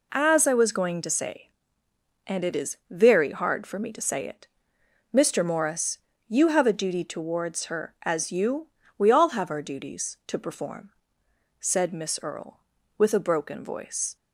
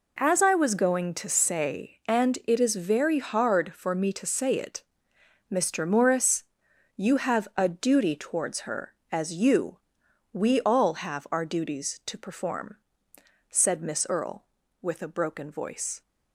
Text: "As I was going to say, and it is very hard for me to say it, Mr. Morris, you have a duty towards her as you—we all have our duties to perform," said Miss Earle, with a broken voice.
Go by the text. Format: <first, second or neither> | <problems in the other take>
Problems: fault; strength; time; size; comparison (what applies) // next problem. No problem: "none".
neither | none